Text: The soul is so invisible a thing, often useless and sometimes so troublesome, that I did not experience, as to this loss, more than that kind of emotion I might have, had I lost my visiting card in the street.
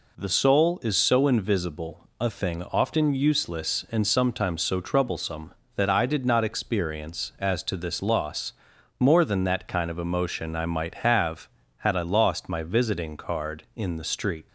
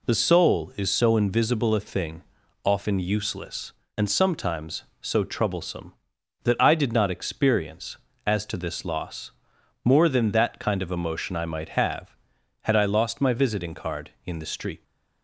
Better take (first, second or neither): neither